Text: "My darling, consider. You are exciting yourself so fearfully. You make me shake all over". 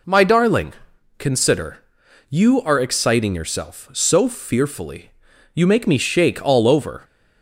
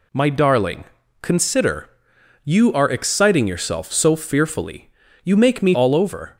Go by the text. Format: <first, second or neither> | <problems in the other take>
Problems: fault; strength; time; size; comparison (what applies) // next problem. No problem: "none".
first | skips "shake"; at 5.7 s